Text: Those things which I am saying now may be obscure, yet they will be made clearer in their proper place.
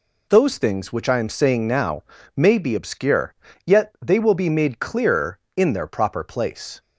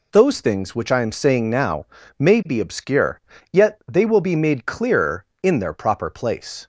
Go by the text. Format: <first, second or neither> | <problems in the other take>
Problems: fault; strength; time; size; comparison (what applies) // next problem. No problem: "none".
neither | pauses between "now" and "may"; slight; the same in both